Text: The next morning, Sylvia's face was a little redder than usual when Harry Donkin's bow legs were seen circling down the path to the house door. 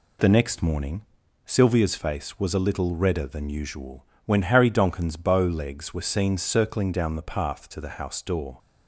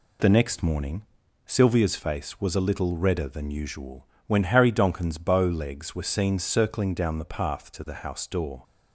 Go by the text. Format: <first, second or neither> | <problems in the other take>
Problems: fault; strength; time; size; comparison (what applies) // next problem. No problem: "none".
neither | pauses between "usual" and "when"; slight; the same in both